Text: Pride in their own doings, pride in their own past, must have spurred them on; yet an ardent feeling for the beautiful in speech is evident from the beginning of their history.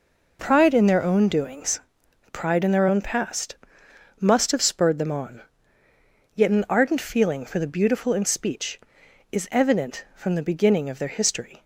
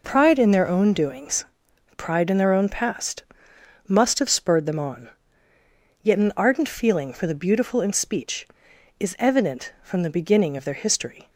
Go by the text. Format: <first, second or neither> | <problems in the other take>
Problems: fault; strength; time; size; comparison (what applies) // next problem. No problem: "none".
neither | none